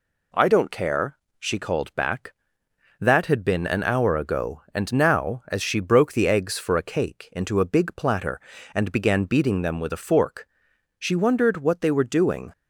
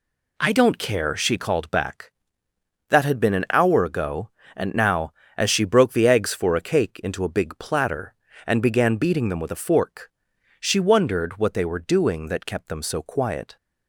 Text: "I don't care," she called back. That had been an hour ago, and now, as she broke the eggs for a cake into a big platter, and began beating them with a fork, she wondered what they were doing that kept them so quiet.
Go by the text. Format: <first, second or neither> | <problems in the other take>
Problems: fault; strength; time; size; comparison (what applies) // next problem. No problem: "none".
second | stops before "that kept them so quiet"; at 12.5 s